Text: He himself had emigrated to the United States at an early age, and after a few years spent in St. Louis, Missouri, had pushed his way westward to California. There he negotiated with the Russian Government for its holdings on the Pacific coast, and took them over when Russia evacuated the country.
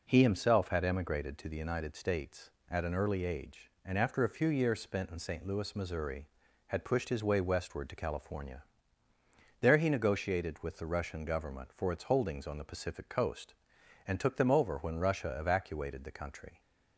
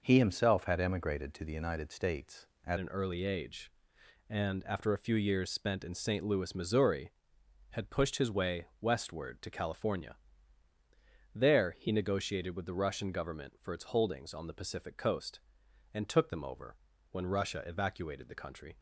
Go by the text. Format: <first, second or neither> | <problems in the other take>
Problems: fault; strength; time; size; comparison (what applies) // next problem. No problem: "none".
first | changes voice at "an"; from 2.7 s on; 16.0 s long // pauses between "over" and "when"; slight; at 16.7 s; 0.34 s long